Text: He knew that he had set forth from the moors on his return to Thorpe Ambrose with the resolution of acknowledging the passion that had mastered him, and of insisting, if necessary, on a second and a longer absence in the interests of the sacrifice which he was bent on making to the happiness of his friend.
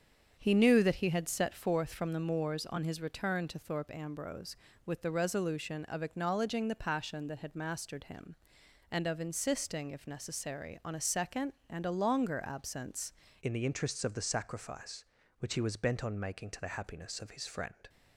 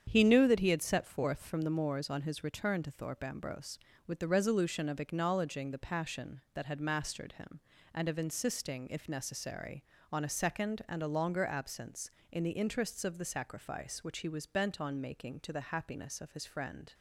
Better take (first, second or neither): second